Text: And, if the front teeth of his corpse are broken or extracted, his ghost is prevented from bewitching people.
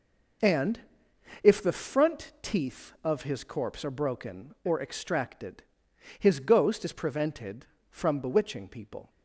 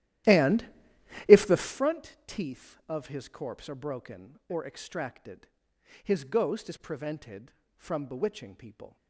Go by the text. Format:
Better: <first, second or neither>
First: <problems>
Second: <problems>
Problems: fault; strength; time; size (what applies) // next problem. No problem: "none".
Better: first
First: none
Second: starts louder than the rest; strong; until 1.9 s; 13.5 dB